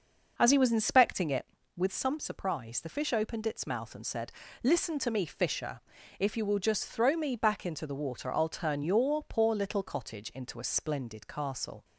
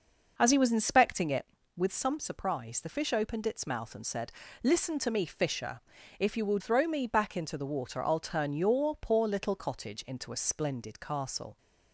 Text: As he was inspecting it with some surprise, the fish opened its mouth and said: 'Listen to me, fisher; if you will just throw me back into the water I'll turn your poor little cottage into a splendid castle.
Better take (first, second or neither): first